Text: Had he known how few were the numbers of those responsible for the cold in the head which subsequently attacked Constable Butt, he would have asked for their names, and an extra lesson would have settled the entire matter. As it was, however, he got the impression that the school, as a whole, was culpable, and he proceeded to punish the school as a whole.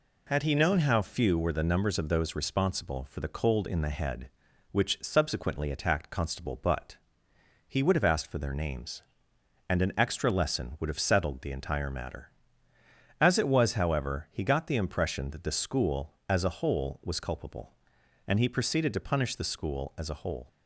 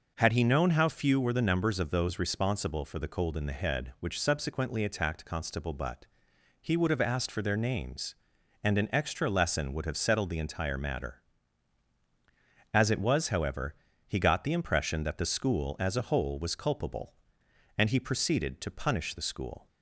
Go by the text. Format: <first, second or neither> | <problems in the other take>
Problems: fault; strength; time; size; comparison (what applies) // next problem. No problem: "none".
first | stops before "as a whole"; at 19.6 s